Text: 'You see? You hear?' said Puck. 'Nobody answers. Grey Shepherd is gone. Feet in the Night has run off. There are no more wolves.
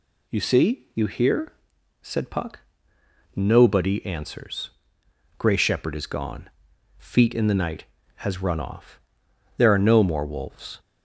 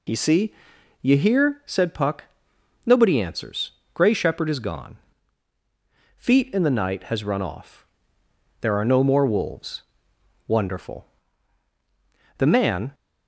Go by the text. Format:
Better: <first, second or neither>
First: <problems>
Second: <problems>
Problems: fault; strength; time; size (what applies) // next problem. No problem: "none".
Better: first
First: none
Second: goes on to say "Wonderful The man"; strong; from 10.4 s on; 2.4 s long